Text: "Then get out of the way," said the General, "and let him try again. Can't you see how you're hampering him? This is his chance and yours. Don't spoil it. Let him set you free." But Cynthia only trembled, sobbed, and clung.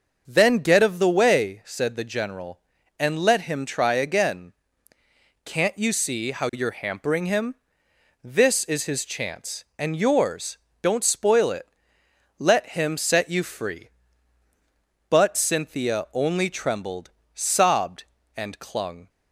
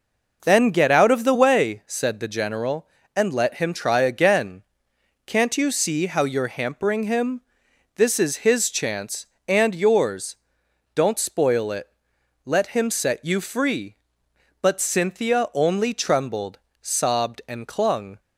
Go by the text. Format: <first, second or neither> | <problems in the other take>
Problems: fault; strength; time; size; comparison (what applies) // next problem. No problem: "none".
second | starts louder than the rest; noticeable; until 1.2 s; 6 dB // skips "out"; at 0.8 s